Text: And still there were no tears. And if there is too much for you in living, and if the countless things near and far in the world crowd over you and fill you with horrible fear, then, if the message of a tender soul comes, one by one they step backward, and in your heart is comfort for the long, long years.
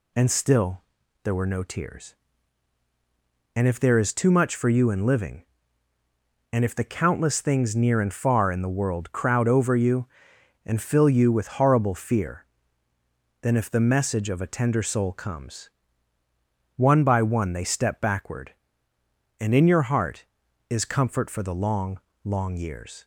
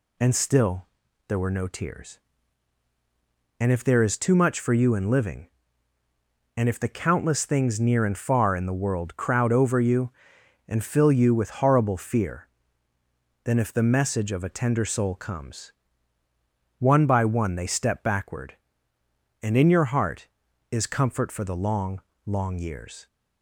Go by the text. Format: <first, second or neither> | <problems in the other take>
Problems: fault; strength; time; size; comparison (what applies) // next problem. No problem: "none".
neither | pauses between "still" and "there"; the same in both